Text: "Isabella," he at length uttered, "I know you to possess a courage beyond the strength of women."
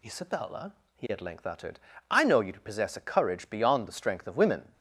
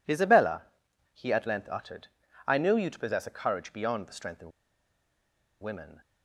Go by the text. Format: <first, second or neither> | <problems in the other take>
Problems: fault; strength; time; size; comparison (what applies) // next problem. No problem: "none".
first | pauses between "of" and "women"; at 4.5 s; 1.1 s long